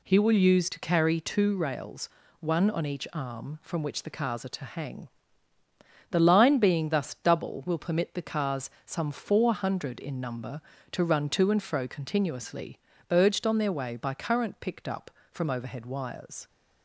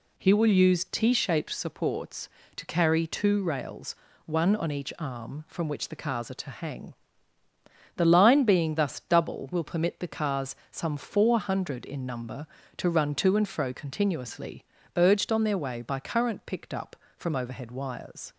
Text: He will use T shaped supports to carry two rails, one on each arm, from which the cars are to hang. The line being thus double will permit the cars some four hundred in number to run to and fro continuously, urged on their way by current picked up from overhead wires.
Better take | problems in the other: second | skips "T shaped supports"; at 0.6 s // pauses between "cars" and "some"; slight; at 8.6 s; 0.16 s long; slight in the second

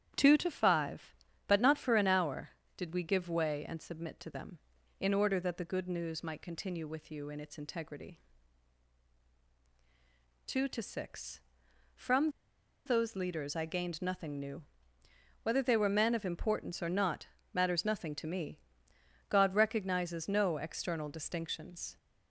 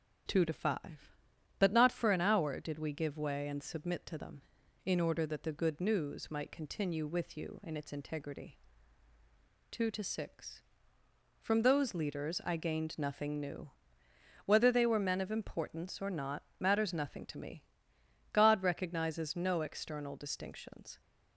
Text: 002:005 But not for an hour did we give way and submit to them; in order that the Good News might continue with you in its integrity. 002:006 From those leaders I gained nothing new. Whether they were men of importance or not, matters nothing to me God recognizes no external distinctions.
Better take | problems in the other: second | starts louder than the rest; strong; until 1.5 s; 10 dB // pauses between "From" and "those"; noticeable; at 12.3 s; 0.55 s long // pauses between "me" and "God"; noticeable; at 18.5 s; 0.72 s long; noticeable in the second

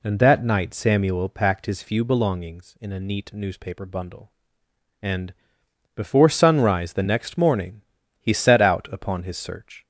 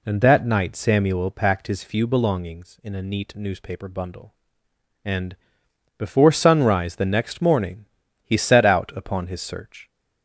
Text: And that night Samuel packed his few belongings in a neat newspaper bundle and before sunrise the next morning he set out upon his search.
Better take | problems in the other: neither | pauses between "and" and "before"; noticeable; the same in both // pauses between "morning" and "he"; slight; the same in both

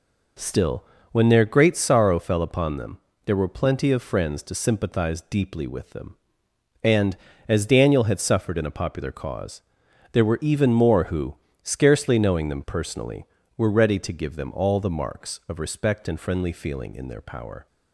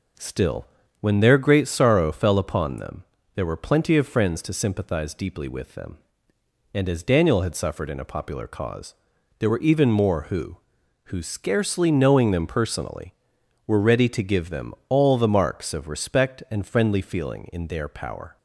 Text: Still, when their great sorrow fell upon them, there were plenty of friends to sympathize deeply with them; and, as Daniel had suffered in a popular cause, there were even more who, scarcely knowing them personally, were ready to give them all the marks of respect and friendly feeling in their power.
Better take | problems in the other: first | says "who" twice; at 11.0 s

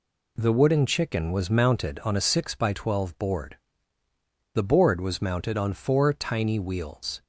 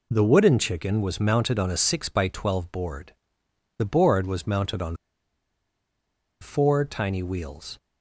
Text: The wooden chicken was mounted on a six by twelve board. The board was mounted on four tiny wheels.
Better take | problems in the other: first | pauses between "on" and "four"; strong; at 4.9 s; 1.4 s long

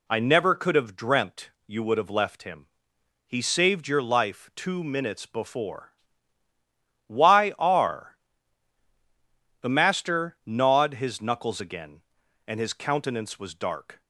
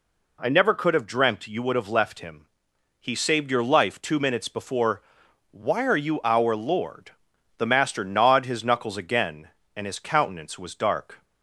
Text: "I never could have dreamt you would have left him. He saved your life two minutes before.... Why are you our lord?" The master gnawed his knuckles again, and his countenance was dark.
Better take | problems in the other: second | pauses between "dreamt" and "you"; slight; at 1.5 s; 0.16 s long // skips "you our lord"; at 8.8 s

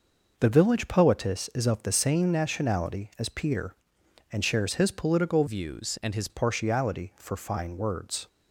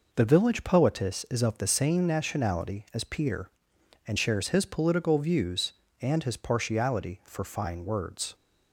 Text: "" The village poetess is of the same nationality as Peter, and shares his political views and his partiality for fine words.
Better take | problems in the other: second | changes voice from "views" to "his"; from 5.4 to 6.2 s; 0.8 s long

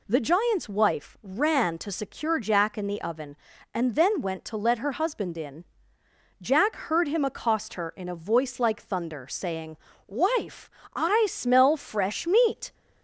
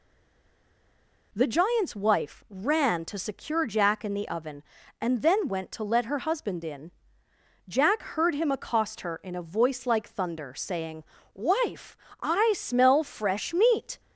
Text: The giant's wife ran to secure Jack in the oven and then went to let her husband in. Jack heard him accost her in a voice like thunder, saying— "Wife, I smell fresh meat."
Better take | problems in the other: first | stays silent before the first word; noticeable; until 1.3 s; 1.3 s long

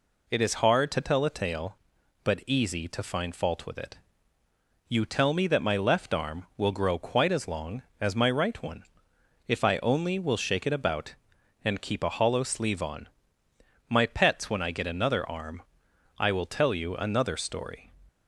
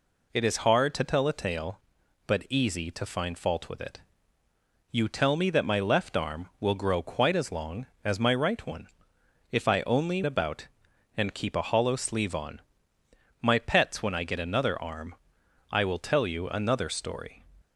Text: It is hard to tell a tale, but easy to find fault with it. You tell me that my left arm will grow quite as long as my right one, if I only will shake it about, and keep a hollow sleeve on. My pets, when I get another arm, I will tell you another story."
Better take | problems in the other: first | skips "will shake it"; at 10.2 s

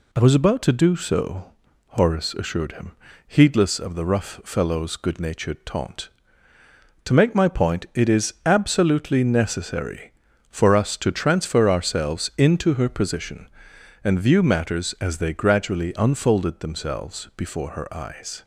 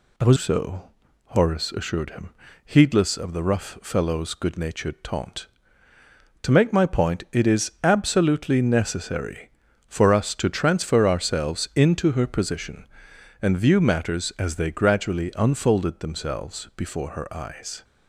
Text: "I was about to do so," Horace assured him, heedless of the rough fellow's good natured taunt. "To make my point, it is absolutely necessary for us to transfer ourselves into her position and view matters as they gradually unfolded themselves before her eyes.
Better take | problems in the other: first | skips "about to do"; at 0.3 s

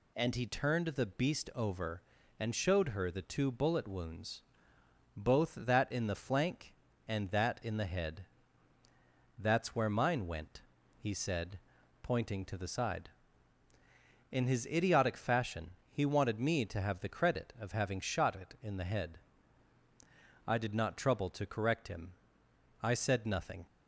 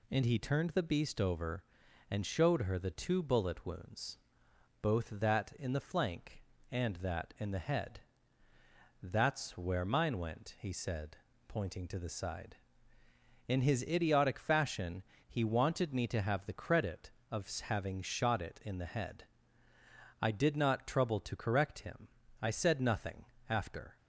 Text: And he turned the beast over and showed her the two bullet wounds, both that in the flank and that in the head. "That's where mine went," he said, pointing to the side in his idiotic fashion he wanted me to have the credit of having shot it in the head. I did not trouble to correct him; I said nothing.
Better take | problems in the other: first | pauses between "fashion" and "he"; slight; at 15.0 s; 0.26 s long; slight in the first // goes on to say "After"; slight; from 23.4 s on; 0.48 s long

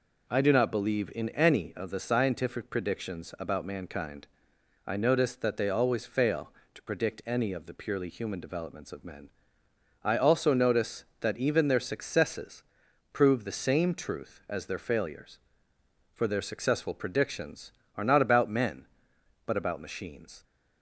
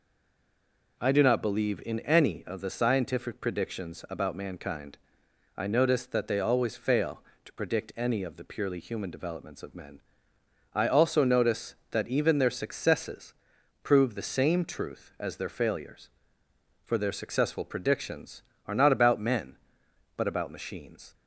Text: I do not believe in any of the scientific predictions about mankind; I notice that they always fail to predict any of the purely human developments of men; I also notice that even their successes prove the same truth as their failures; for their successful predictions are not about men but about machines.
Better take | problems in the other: first | stays silent before the first word; until 0.9 s; 0.9 s long // pauses between "successes" and "prove"; noticeable; at 13.3 s; 0.50 s long; noticeable in the first

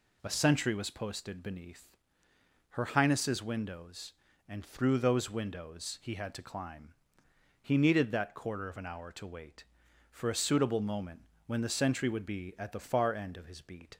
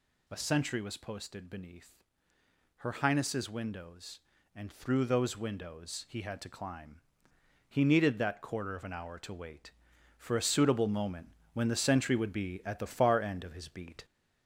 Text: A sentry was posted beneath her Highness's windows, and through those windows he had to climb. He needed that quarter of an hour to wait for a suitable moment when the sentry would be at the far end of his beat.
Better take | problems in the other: first | gets louder; noticeable; throughout; 4 dB // pauses between "beneath" and "her"; noticeable; at 2.0 s; 0.78 s long; noticeable in the first // pauses between "moment" and "when"; slight; at 11.2 s; 0.24 s long; slight in the first

